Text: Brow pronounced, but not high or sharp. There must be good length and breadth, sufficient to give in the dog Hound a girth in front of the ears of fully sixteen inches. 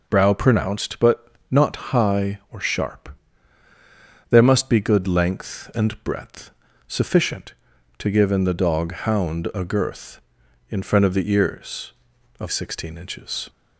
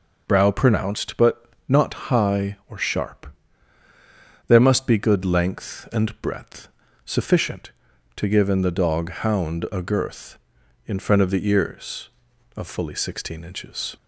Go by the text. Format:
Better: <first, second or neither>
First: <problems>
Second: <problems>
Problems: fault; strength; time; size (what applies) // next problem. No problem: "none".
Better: second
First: pauses between "but" and "not"; slight; at 1.2 s; 0.24 s long // pauses between "not" and "high"; slight; at 1.7 s; 0.16 s long // skips "fully"; at 12.4 s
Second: pauses between "but" and "not"; slight; at 1.4 s; 0.24 s long // pauses between "not" and "high"; slight; at 1.9 s; 0.16 s long